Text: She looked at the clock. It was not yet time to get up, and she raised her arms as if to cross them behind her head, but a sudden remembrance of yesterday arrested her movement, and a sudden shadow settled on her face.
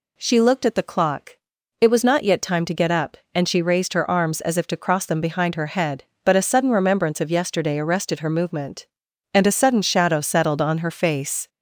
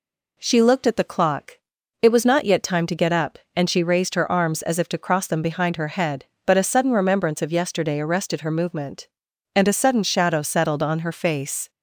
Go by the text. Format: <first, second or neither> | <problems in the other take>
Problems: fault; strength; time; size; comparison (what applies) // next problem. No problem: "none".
second | gets louder; slight; throughout; 3 dB